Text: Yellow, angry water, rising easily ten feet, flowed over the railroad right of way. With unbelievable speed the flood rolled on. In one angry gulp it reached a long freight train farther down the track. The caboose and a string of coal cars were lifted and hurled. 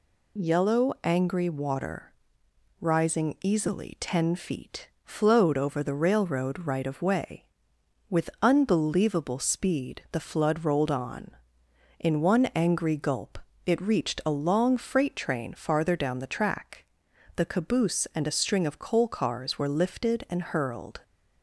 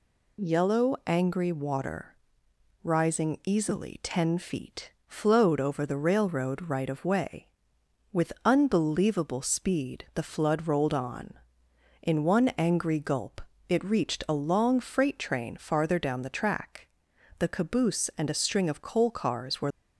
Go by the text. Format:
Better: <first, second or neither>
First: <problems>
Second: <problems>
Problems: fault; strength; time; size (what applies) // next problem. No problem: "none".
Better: first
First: pauses between "gulp" and "it"; slight; at 13.3 s; 0.26 s long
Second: pauses between "gulp" and "it"; slight; at 13.4 s; 0.26 s long // stops before "lifted and hurled"; at 19.7 s